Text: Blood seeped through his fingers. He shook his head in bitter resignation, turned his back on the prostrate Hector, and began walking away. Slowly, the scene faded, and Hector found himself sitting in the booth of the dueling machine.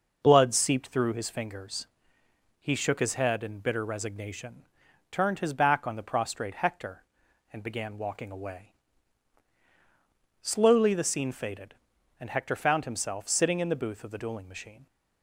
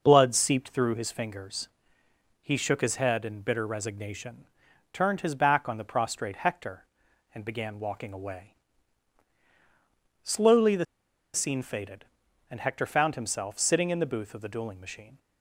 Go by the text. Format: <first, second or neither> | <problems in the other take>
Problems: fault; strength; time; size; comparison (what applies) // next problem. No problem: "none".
first | pauses between "the" and "scene"; noticeable; at 10.8 s; 0.49 s long